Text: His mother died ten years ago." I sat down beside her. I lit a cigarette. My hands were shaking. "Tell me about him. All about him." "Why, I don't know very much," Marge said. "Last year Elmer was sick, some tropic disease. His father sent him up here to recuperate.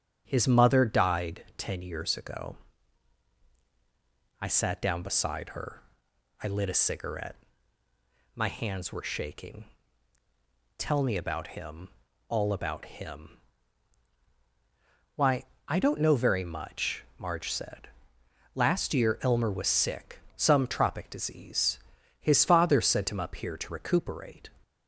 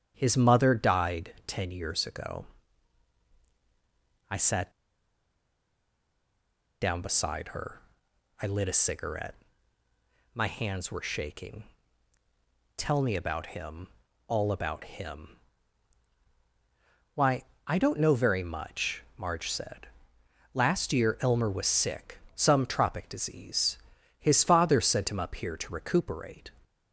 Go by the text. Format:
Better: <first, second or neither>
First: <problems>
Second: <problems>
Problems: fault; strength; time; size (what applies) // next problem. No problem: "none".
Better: first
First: starts louder than the rest; strong; until 1.2 s; 9 dB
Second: starts louder than the rest; strong; until 1.1 s; 9 dB // pauses between "sat" and "down"; strong; at 4.7 s; 2.1 s long